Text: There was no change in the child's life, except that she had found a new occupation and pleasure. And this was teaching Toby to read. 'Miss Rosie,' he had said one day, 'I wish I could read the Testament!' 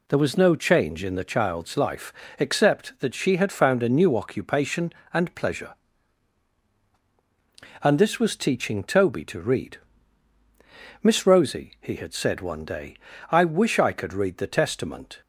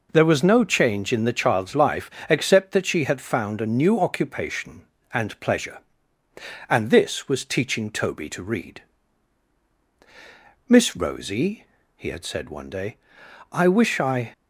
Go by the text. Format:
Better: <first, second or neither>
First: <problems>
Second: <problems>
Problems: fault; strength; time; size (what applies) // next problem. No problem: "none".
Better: first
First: none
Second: stops before "could read the Testament"; at 14.3 s